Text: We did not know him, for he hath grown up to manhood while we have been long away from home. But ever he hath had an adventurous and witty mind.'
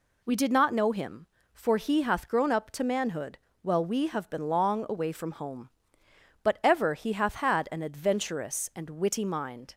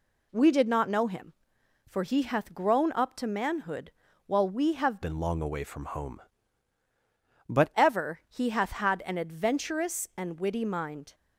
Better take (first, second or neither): first